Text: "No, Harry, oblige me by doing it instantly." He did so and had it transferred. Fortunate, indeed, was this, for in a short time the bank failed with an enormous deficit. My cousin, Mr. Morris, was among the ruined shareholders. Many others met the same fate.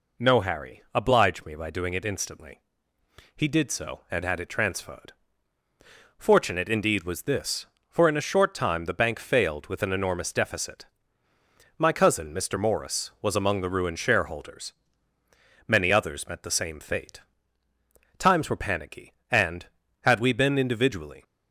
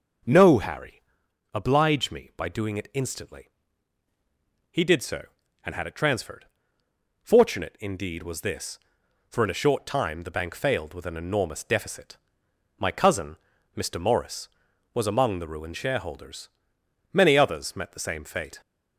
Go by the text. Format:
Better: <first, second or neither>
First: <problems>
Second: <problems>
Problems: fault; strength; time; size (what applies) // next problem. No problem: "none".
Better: second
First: goes on to say "Times were panicky and had we been individually"; strong; from 18.1 s on; 3.0 s long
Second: none